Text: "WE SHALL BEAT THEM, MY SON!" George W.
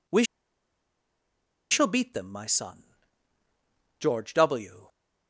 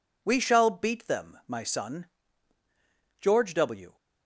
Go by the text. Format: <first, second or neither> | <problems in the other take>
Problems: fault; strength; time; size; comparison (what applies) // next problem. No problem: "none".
second | pauses between "WE" and "SHALL"; strong; at 0.2 s; 1.4 s long